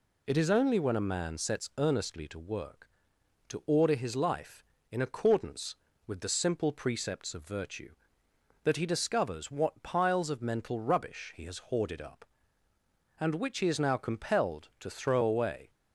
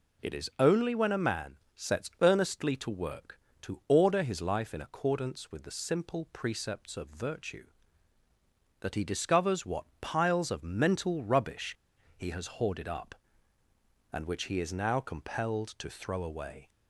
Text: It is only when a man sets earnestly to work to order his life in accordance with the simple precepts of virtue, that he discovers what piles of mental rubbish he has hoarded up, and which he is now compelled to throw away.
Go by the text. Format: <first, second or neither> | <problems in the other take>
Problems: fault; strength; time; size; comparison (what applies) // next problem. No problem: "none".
first | pauses between "man" and "sets"; slight; at 1.5 s; 0.18 s long // pauses between "rubbish" and "he"; at 11.7 s; 0.41 s long